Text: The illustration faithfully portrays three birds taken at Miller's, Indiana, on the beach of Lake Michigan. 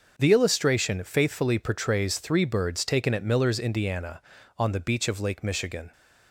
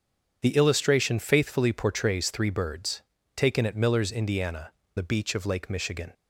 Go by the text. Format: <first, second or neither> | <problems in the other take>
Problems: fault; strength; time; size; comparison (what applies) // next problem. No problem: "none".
first | starts louder than the rest; strong; until 1.4 s; 7.5 dB; also in the first // pauses between "birds" and "taken"; slight; at 3.0 s; 0.34 s long // skips "on"; at 4.8 s